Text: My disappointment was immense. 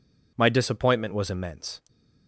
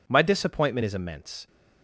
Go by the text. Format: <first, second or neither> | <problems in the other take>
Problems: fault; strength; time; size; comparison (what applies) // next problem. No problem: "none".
first | says "is" for "was"; at 0.8 s